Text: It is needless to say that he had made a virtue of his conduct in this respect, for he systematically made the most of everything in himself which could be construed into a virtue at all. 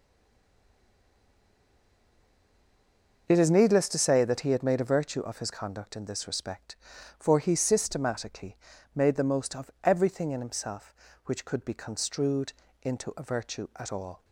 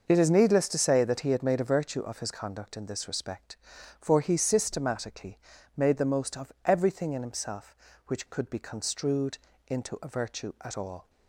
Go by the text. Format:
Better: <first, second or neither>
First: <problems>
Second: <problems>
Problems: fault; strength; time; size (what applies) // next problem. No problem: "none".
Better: second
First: stays silent before the first word; strong; until 3.2 s; 3.2 s long // pauses between "systematically" and "made"; at 8.5 s; 0.40 s long // pauses between "construed" and "into"; slight; at 12.5 s; 0.30 s long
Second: pauses between "systematically" and "made"; at 5.3 s; 0.40 s long // pauses between "construed" and "into"; slight; at 9.3 s; 0.30 s long